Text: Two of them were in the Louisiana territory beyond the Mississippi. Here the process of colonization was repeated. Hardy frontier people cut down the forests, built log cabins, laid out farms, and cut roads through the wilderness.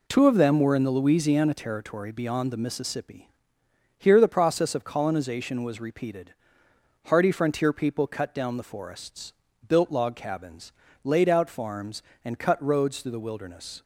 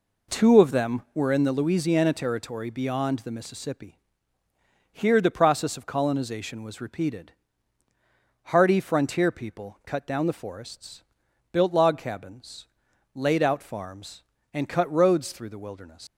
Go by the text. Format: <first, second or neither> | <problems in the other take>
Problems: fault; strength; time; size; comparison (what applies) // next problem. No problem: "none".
first | leaves "wilderness" unfinished; at 16.0 s; 125 ms